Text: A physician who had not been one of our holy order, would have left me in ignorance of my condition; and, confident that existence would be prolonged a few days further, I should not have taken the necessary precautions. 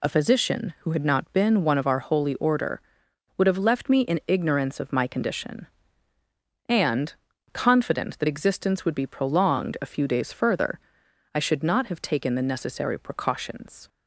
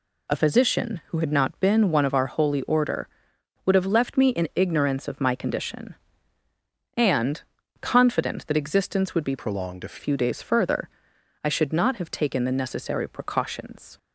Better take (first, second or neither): first